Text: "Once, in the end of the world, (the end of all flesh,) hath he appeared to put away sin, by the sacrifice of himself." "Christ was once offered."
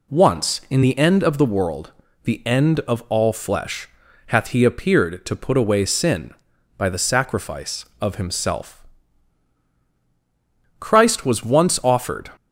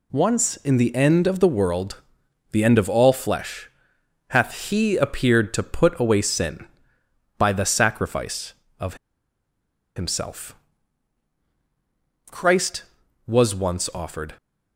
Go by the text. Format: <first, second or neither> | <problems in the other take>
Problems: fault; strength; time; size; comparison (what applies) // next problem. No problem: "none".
first | pauses between "of" and "himself"; at 8.9 s; 1.0 s long